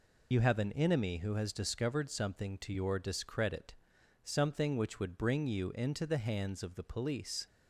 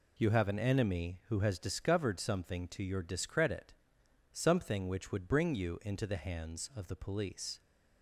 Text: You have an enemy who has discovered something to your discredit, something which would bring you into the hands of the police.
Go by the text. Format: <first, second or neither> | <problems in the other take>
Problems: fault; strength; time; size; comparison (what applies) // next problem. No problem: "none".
second | loses the start of "You"; at 0.3 s; 35 ms